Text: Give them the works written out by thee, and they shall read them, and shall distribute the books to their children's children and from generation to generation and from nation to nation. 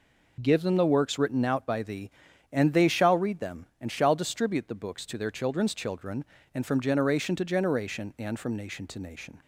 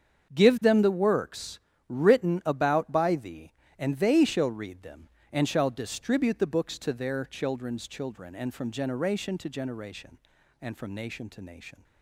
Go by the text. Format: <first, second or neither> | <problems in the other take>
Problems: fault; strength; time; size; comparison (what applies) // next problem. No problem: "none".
first | starts louder than the rest; strong; until 1.3 s; 7 dB // pauses between "works" and "written"; slight; at 1.5 s; 0.28 s long // says "about" for "out"; at 2.4 s